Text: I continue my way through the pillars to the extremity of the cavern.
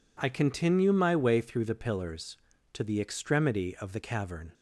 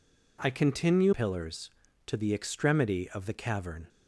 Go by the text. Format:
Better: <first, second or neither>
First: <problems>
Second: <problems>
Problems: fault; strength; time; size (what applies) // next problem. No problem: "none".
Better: first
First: none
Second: skips "my way through the"; at 1.1 s